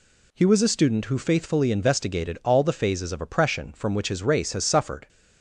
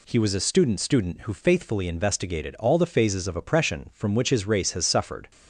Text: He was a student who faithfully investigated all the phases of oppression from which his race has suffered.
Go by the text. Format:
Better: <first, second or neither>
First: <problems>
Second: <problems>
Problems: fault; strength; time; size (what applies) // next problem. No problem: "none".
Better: first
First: none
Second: says "student" twice; at 0.8 s